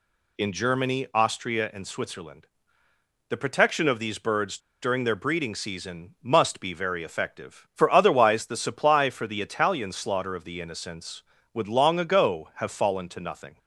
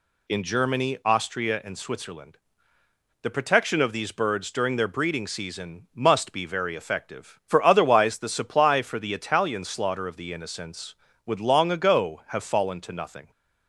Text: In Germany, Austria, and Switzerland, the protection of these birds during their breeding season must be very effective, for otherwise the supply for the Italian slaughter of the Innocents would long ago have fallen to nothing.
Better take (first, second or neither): second